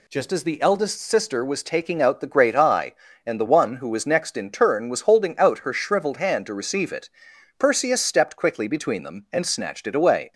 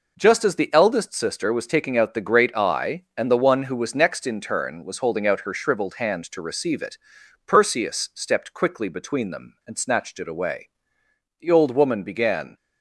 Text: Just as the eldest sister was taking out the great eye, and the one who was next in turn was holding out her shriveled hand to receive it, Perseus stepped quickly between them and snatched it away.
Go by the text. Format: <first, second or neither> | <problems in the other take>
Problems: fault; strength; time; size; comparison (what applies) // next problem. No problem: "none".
first | goes on to say "The old woman began"; noticeable; from 11.3 s on; 1.1 s long